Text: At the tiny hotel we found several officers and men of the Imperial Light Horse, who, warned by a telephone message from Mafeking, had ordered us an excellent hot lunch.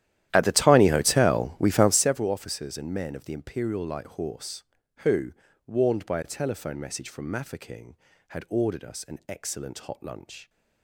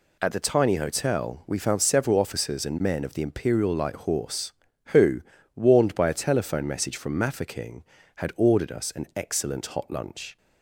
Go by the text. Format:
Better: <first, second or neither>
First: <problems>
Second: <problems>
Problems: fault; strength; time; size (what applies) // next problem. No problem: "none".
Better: second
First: starts louder than the rest; strong; until 2.2 s; 12.5 dB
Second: none